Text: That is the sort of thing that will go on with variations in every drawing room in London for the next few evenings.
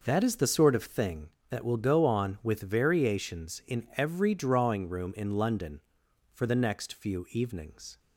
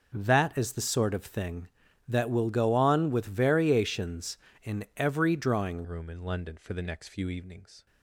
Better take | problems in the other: first | changes voice at "room"; from 5.8 s on; 2.0 s long

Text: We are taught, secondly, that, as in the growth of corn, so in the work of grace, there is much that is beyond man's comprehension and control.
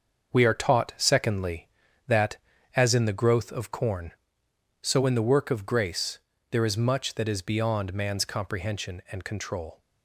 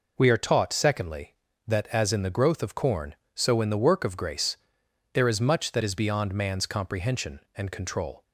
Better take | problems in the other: second | gets quieter; strong; throughout; 7.5 dB

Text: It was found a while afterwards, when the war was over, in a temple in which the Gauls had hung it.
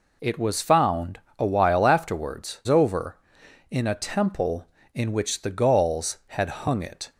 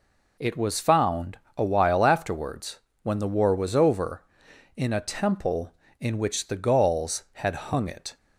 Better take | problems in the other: second | pauses between "found" and "a"; slight; at 1.1 s; 0.18 s long; slight in the second // skips "when the war was"; at 2.6 s

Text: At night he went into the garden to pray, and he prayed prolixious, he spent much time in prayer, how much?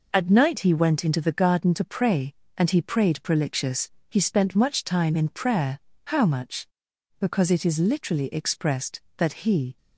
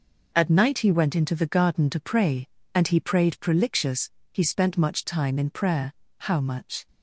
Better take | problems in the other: second | goes on to say "Because it is literally expressed that he"; strong; from 7.1 s on; 2.5 s long

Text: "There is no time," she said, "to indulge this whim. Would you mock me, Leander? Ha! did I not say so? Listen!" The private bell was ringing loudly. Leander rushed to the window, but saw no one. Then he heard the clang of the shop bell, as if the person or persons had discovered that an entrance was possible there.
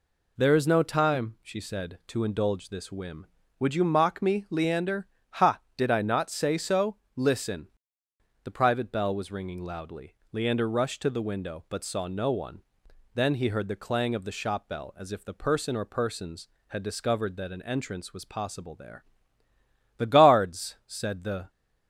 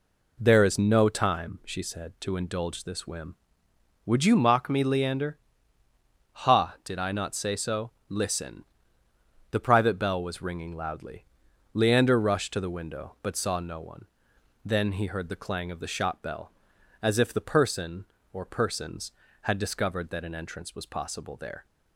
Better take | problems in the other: second | goes on to say "The guards said the"; from 19.9 s on; 1.5 s long

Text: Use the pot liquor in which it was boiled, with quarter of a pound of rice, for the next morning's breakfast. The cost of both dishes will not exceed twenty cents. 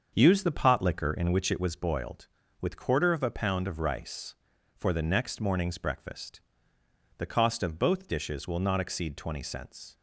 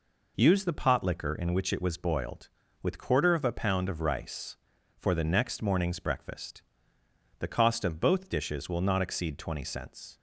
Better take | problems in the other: second | starts louder than the rest; until 1.7 s; 6.5 dB

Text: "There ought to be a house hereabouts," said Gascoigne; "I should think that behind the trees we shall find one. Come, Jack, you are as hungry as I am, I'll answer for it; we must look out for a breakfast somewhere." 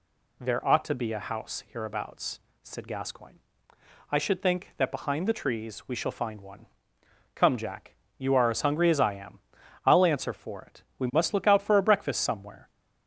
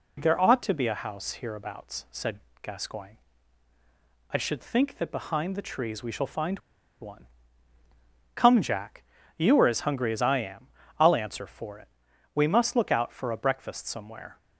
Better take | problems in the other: first | pauses between "said" and "Gascoigne"; slight; at 2.4 s; 0.22 s long // pauses between "find" and "one"; at 6.5 s; 0.42 s long

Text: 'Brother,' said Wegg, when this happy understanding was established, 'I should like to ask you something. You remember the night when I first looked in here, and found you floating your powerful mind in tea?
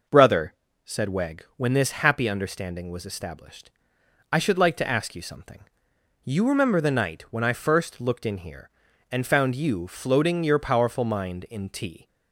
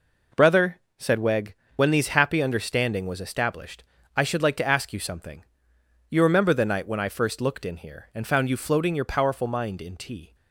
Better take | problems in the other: first | says "these" for "this"; at 1.9 s

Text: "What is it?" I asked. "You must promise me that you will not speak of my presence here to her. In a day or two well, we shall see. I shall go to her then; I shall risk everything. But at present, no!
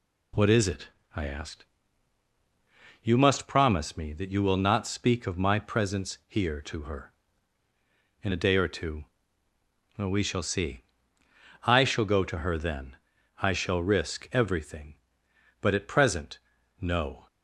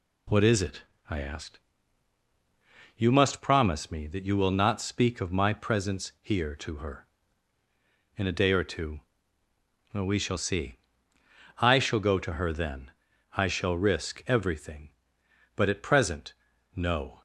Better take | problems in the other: neither | pauses between "two" and "well"; noticeable; the same in both

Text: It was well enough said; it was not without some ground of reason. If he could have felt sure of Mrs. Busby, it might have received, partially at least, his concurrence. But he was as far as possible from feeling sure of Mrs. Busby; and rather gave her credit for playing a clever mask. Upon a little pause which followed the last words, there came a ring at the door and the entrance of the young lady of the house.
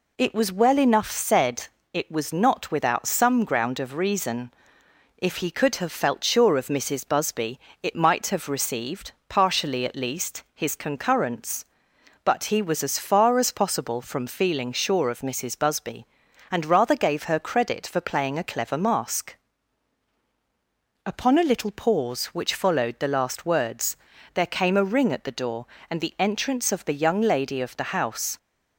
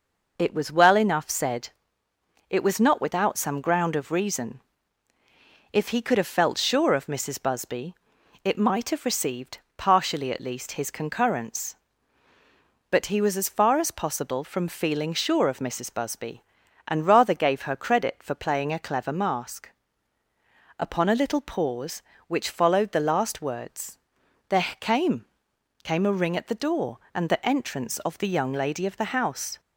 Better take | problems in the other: first | pauses between "there" and "came"; slight; at 24.6 s; 0.16 s long // says "came" twice; at 25.8 s

